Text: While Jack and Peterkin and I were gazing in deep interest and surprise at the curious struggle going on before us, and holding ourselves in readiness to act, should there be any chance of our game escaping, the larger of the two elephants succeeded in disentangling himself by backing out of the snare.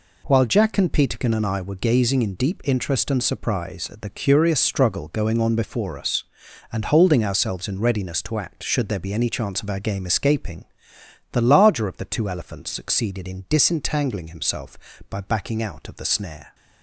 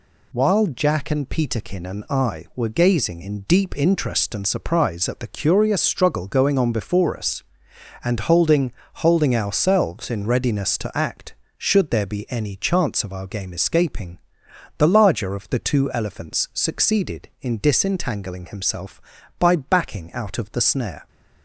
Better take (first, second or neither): first